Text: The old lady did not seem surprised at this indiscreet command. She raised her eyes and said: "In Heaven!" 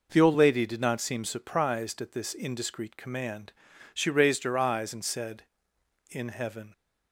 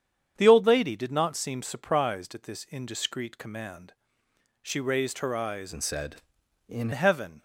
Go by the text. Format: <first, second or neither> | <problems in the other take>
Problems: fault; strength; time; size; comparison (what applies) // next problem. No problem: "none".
first | starts louder than the rest; strong; until 1.3 s; 8 dB // changes voice from "and" to "In"; from 5.7 to 6.9 s; 1.2 s long